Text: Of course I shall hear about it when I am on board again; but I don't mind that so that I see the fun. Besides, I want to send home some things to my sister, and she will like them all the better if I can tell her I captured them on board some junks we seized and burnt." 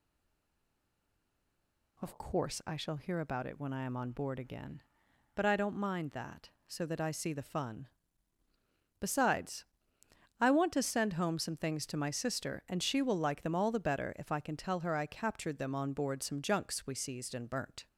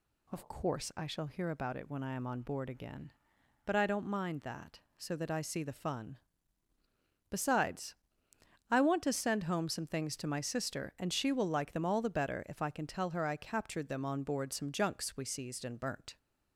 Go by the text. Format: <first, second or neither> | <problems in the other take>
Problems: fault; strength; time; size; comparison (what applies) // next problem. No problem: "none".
second | stays silent before the first word; noticeable; until 1.9 s; 1.9 s long